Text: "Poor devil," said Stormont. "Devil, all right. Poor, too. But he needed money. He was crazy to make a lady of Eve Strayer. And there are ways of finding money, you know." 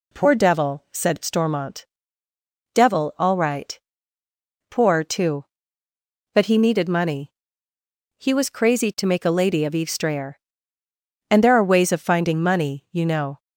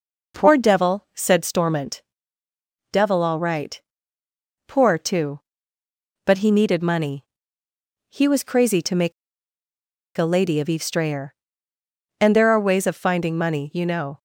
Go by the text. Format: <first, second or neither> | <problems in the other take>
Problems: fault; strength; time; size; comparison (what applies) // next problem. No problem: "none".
first | pauses between "make" and "a"; at 9.1 s; 1.0 s long